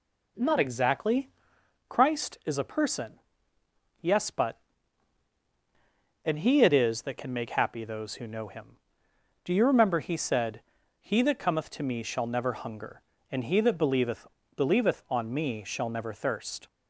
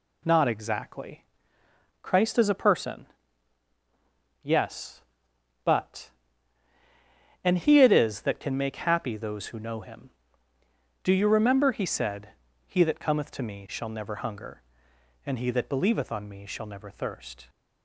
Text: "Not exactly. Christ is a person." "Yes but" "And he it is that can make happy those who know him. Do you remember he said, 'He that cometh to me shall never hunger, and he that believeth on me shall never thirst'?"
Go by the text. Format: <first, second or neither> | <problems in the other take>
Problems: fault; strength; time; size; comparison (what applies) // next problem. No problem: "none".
second | says "believeth" twice; at 14.5 s